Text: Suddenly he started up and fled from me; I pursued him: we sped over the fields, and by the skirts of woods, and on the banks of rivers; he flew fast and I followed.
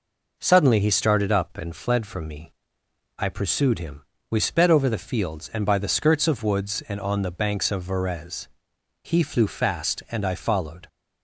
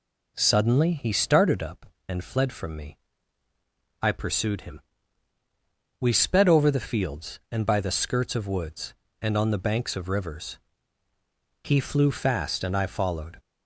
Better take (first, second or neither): second